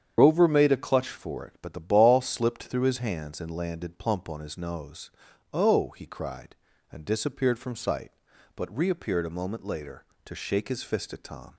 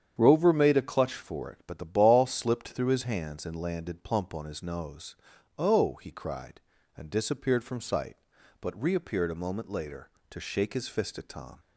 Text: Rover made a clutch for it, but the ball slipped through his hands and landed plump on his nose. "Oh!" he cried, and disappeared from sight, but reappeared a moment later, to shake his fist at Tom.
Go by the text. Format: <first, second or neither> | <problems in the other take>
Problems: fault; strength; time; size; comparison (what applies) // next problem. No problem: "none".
second | loses the start of "Rover"; at 0.1 s; 60 ms // starts louder than the rest; strong; until 1.1 s; 8.5 dB; strong in the second